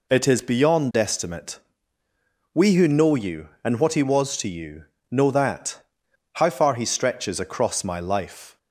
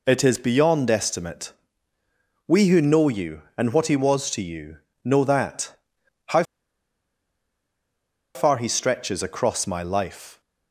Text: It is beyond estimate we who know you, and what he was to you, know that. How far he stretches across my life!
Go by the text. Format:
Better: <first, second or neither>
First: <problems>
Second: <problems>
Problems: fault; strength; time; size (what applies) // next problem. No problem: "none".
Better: first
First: pauses between "estimate" and "we"; noticeable; at 1.5 s; 0.94 s long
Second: pauses between "estimate" and "we"; noticeable; at 1.5 s; 0.94 s long // pauses between "How" and "far"; strong; at 6.4 s; 1.9 s long